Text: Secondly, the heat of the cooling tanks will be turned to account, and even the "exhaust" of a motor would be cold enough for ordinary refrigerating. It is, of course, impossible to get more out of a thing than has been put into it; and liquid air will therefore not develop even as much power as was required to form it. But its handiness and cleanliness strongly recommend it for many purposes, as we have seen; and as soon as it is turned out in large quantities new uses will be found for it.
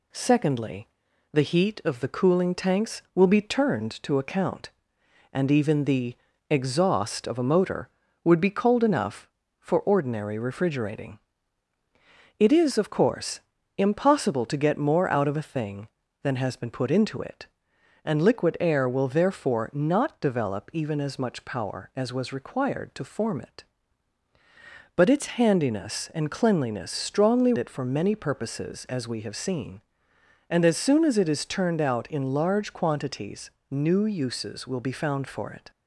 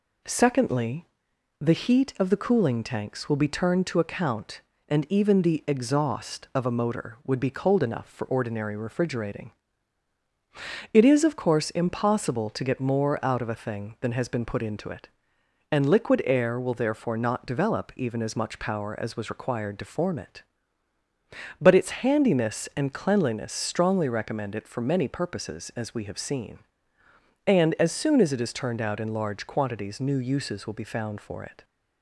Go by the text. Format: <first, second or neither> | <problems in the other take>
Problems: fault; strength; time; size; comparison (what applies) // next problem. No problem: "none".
second | pauses between "the" and "exhaust"; slight; at 6.1 s; 0.34 s long // skips "recommend"; at 27.5 s // pauses between "quantities" and "new"; slight; at 33.5 s; 0.20 s long